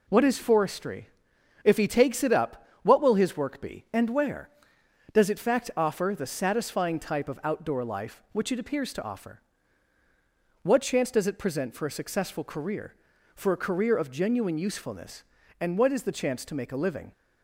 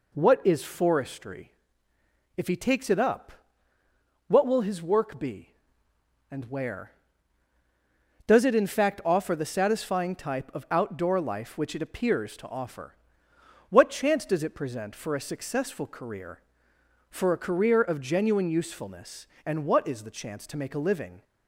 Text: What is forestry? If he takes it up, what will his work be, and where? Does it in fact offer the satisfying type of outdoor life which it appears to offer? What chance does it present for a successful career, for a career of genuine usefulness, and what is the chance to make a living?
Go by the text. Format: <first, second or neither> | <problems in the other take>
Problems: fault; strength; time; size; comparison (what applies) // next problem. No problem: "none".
second | skips "in"; at 5.3 s